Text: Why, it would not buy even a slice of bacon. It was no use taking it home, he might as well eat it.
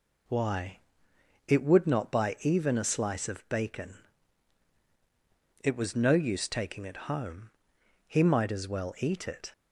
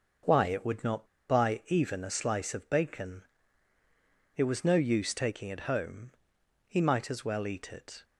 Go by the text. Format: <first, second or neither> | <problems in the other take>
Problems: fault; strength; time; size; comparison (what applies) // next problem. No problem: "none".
first | pauses between "not" and "buy"; slight; at 1.0 s; 0.24 s long